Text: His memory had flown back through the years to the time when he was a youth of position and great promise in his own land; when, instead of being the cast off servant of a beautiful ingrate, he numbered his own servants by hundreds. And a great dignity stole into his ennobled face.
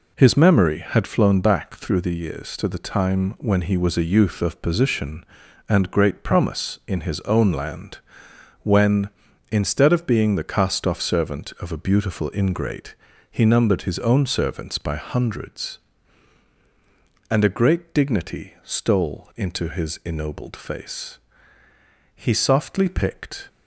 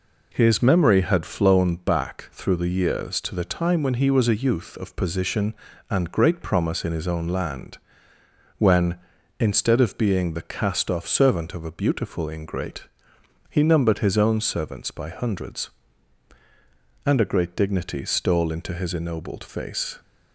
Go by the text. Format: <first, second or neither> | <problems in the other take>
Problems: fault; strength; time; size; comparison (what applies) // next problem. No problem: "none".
second | goes on to say "He softly picked"; from 22.1 s on; 1.3 s long